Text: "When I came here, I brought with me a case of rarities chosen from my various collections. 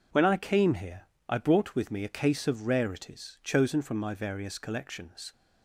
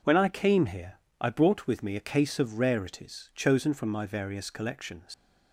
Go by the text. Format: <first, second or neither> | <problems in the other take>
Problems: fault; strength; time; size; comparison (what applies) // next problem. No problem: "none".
first | leaves "collections" unfinished; at 5.1 s; 95 ms